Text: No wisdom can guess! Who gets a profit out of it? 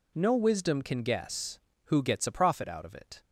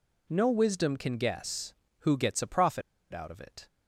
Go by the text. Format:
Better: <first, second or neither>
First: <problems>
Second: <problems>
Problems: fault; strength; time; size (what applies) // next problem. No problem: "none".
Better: first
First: none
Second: pauses between "profit" and "out"; slight; at 2.8 s; 0.30 s long